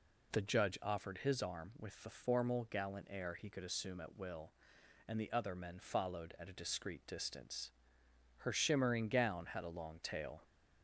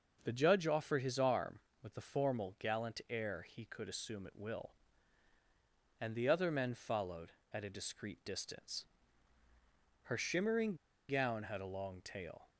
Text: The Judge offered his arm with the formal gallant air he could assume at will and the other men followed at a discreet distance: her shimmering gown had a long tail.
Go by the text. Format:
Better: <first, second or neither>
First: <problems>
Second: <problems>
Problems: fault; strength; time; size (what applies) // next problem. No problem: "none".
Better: first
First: none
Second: starts louder than the rest; until 1.2 s; 6 dB // pauses between "shimmering" and "gown"; slight; at 10.7 s; 0.33 s long